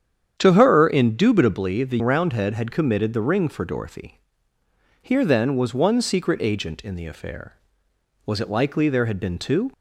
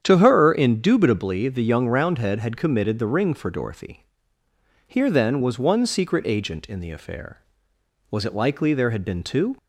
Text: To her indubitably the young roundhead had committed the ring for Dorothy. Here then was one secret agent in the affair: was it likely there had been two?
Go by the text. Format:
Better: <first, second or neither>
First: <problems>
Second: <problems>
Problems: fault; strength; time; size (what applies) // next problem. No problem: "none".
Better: second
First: starts louder than the rest; strong; until 1.3 s; 8.5 dB // skips "young"; at 2.0 s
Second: starts louder than the rest; strong; until 1.0 s; 8.5 dB